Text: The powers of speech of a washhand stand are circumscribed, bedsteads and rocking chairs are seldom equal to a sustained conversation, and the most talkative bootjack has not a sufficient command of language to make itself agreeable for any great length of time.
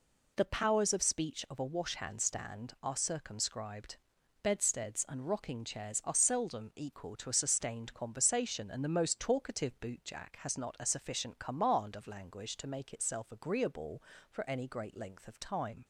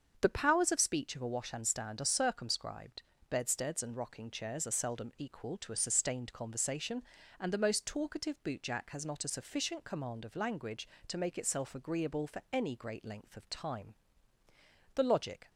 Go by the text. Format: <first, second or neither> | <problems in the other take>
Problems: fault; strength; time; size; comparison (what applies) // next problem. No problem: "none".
first | starts louder than the rest; until 1.2 s; 7 dB // goes on to say "The logic"; from 14.9 s on; 0.56 s long